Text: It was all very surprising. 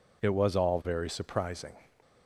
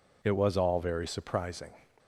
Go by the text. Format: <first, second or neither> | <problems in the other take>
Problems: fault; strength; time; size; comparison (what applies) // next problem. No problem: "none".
neither | none